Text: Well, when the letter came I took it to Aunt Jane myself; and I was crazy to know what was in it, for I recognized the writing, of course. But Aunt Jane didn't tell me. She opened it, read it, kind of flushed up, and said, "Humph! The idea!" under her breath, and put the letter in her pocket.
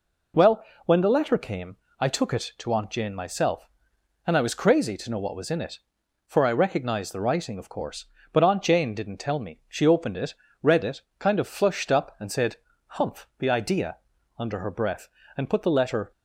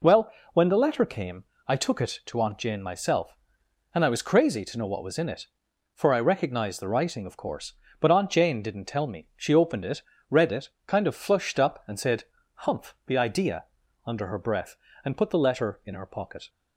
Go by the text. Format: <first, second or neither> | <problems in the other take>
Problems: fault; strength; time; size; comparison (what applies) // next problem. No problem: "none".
second | pauses between "came" and "I"; slight; at 1.7 s; 0.20 s long; slight in the second // stops before "in her pocket"; at 16.1 s